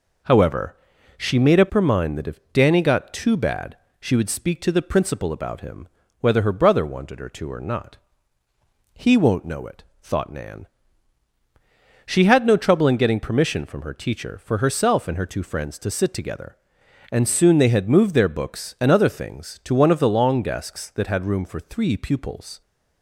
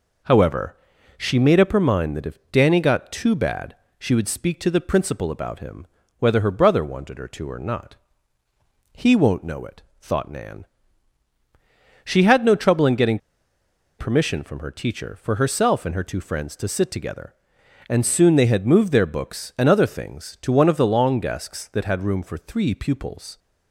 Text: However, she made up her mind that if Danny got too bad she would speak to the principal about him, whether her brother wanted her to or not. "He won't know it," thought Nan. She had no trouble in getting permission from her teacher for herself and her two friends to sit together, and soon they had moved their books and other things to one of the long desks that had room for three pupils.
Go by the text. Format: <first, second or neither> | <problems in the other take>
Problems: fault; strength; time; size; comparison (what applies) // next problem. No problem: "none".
first | pauses between "bad" and "she"; slight; at 3.7 s; 0.24 s long; slight in the first // pauses between "getting" and "permission"; noticeable; at 13.1 s; 0.81 s long